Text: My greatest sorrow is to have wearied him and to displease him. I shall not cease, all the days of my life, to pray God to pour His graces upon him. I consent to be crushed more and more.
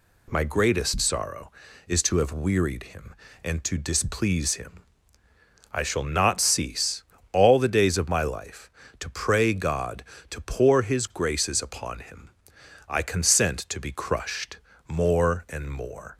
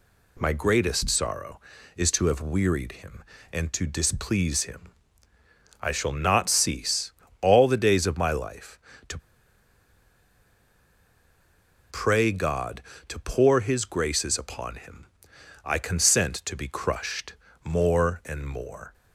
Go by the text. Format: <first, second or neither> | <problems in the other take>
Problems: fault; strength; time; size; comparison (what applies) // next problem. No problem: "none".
first | pauses between "to" and "pray"; strong; at 9.1 s; 2.7 s long // pauses between "crushed" and "more"; slight; at 17.3 s; 0.30 s long; slight in the first